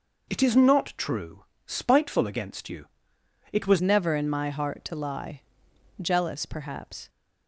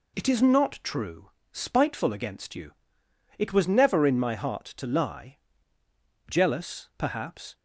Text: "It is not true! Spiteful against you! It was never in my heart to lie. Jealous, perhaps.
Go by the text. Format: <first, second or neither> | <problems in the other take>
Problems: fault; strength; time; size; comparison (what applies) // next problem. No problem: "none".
second | changes voice at "never"; from 3.8 s on; 3.2 s long